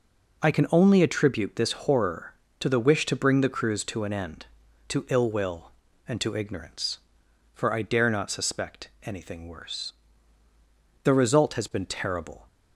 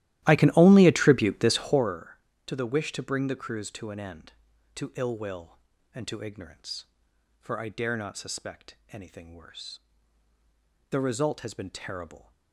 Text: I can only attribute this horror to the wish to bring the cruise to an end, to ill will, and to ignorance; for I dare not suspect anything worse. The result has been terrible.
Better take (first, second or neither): first